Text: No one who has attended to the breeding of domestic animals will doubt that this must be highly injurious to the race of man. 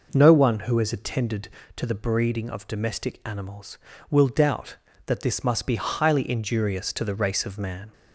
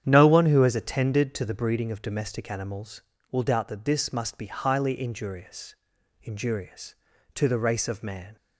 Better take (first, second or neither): first